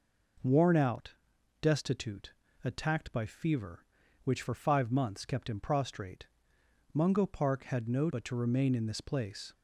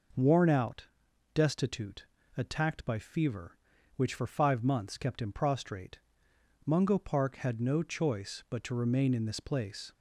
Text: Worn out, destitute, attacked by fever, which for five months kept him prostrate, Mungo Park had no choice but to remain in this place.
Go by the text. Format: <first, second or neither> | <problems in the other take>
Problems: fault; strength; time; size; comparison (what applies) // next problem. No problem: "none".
second | skips "choice"; at 8.0 s